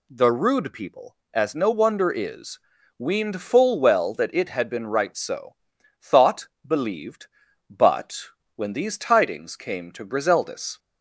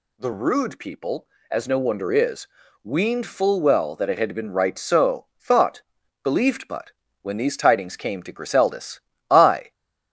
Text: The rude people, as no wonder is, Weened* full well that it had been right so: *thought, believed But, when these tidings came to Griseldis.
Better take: first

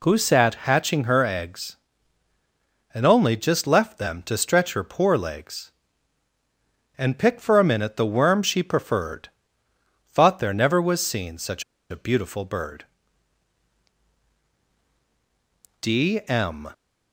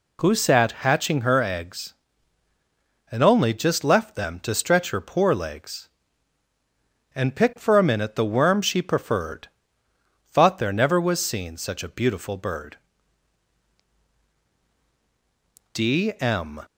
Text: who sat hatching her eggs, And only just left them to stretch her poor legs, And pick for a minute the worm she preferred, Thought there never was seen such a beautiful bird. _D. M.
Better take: second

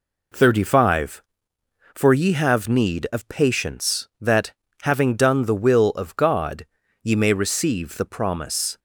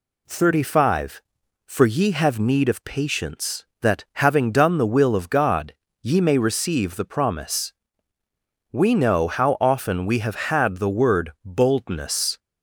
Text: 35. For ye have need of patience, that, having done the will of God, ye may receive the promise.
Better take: first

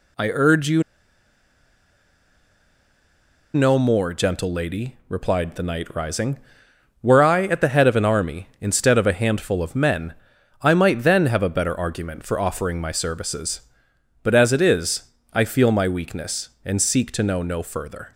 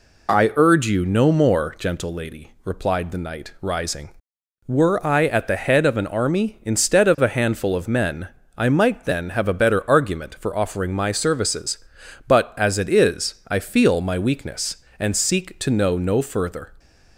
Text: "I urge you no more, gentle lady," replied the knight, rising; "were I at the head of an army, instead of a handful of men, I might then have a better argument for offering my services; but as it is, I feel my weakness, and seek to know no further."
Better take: second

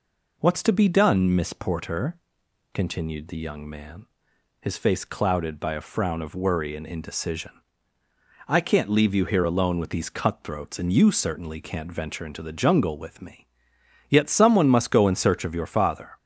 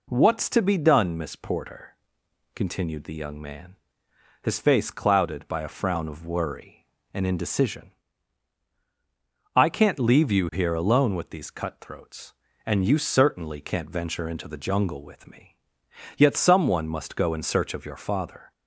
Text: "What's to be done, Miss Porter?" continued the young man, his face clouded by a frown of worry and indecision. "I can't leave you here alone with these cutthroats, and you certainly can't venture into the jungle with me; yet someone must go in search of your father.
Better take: neither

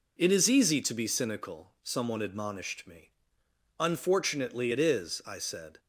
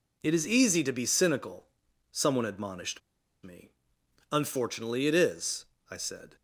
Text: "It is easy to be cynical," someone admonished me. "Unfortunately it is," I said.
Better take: first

